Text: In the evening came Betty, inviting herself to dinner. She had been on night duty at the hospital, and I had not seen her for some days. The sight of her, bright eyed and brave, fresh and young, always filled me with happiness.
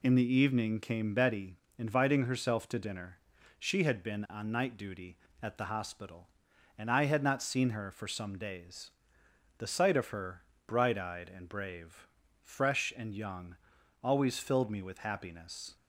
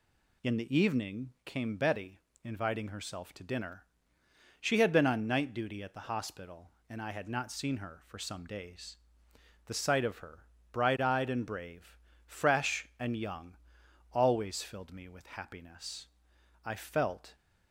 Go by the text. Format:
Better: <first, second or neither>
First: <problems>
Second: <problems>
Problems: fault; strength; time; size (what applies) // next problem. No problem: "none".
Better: first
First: none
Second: goes on to say "I felt"; noticeable; from 16.6 s on; 0.70 s long